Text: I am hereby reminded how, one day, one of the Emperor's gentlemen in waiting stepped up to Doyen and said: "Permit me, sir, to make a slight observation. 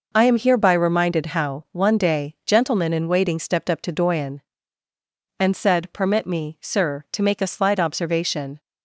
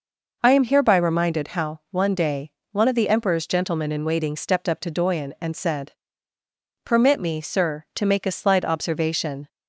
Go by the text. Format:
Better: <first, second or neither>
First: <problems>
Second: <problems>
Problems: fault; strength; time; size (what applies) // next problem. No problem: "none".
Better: second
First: skips "one of the Emperor's"; at 2.4 s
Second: none